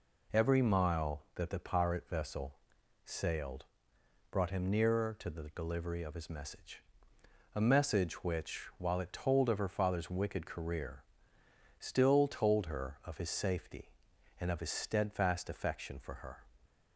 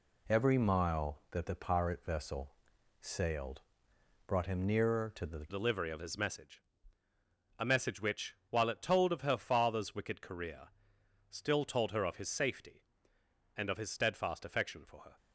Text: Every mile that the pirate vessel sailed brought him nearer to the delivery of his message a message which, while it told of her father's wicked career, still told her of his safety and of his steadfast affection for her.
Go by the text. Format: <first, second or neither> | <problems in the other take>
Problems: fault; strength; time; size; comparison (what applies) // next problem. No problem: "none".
first | pauses between "vessel" and "sailed"; noticeable; at 2.5 s; 0.48 s long; noticeable in the first // pauses between "sailed" and "brought"; noticeable; at 3.5 s; 0.66 s long; noticeable in the first // changes voice at "delivery"; from 5.4 s on; 9.7 s long // pauses between "message" and "a"; noticeable; at 6.6 s; 0.98 s long; noticeable in the first